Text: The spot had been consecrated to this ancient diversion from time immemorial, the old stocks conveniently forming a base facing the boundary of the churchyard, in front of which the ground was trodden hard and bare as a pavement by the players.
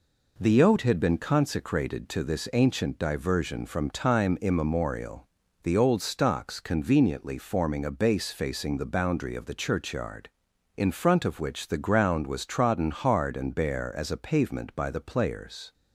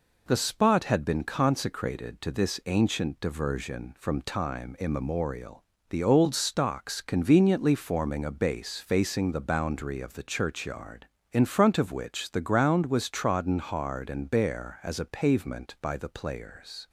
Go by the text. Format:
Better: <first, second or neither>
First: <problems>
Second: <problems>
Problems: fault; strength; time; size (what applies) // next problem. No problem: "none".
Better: second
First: says "oat" for "spot"; at 0.6 s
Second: none